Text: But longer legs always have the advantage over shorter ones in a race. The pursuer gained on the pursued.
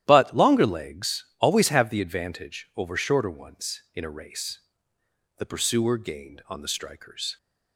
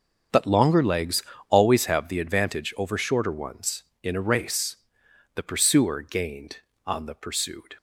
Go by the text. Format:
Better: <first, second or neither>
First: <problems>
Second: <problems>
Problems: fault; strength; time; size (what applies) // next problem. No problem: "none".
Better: second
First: starts louder than the rest; strong; until 1.0 s; 12 dB // pauses between "legs" and "always"; slight; at 1.2 s; 0.16 s long // says "strikers" for "pursued"; at 6.6 s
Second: starts louder than the rest; until 1.5 s; 6.5 dB // pauses between "legs" and "always"; slight; at 1.2 s; 0.26 s long